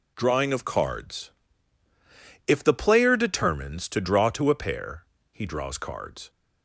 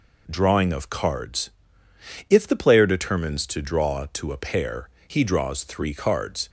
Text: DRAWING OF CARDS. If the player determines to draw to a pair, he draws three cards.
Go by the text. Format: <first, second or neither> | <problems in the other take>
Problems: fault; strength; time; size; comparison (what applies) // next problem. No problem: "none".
second | skips "three"; at 5.7 s